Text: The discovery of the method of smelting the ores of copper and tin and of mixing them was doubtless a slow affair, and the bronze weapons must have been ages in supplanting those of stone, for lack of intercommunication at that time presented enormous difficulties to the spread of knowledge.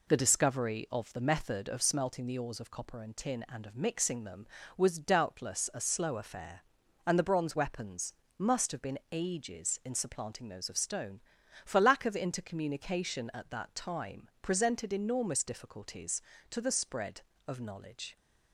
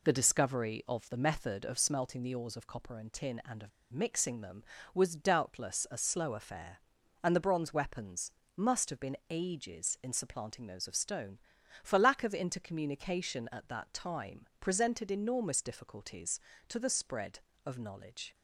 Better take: first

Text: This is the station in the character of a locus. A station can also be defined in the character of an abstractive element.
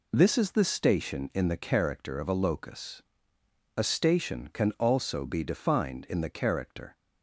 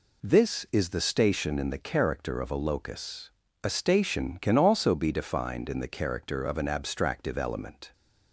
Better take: second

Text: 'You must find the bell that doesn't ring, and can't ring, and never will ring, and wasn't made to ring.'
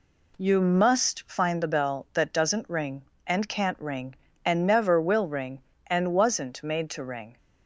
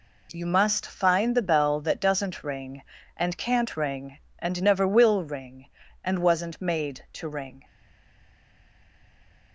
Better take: first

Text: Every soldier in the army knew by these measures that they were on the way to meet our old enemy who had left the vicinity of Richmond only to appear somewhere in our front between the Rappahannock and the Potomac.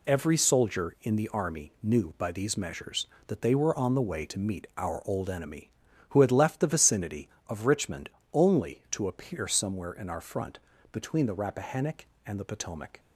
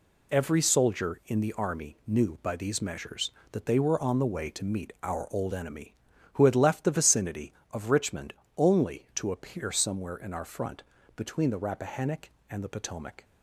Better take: neither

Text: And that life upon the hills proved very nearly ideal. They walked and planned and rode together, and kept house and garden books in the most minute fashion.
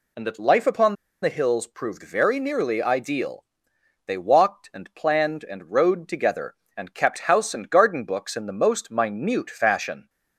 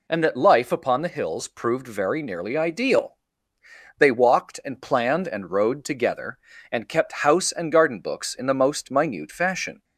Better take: second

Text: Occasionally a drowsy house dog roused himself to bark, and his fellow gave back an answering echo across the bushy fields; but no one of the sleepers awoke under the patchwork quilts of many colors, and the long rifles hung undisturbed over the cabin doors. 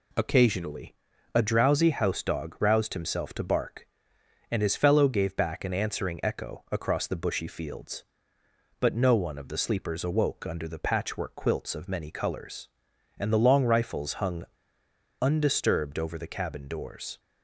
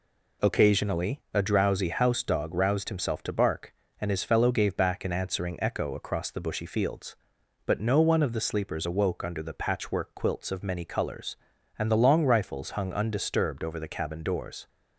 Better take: second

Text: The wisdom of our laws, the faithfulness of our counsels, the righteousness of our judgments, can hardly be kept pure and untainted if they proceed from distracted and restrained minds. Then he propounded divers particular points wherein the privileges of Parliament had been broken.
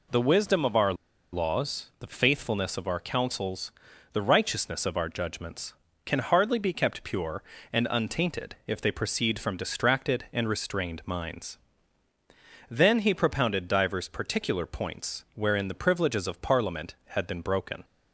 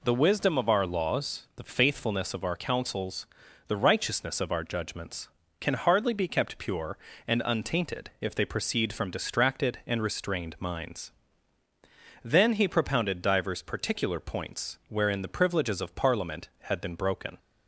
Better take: second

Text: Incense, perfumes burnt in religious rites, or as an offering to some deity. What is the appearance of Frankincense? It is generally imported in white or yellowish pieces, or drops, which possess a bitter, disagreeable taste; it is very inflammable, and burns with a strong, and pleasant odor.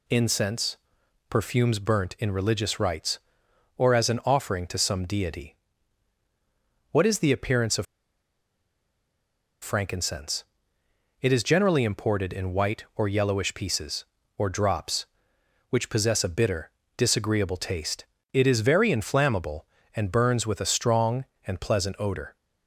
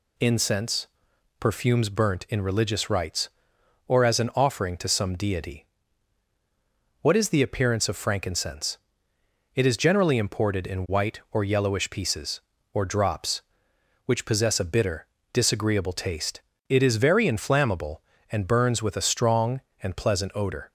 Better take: second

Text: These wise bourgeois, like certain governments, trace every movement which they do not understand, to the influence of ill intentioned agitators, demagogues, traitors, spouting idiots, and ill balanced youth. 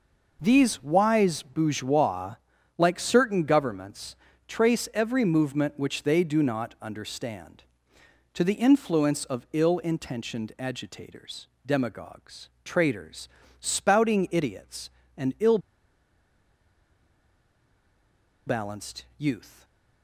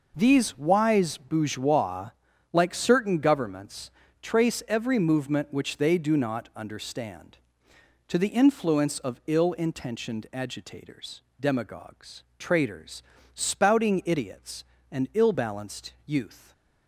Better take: second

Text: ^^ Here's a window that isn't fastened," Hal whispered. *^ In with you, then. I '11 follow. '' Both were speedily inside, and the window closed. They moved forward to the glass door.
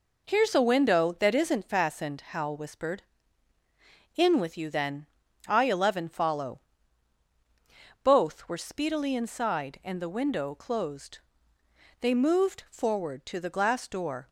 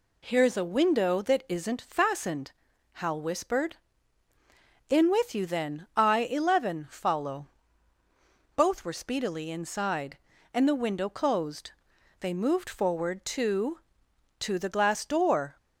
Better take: first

